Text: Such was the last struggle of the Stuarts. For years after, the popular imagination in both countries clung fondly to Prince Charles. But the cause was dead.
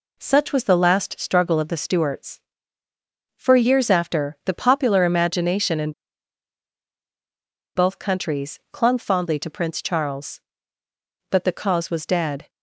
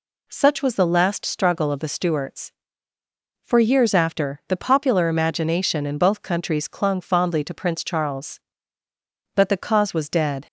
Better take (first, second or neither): second